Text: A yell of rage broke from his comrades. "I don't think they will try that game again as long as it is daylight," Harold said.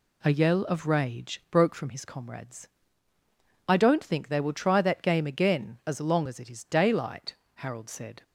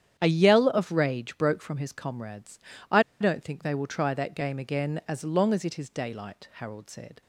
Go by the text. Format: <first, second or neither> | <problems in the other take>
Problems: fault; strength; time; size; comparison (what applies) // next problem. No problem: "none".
first | starts louder than the rest; strong; until 1.1 s; 9.5 dB // pauses between "I" and "don't"; slight; at 3.0 s; 0.18 s long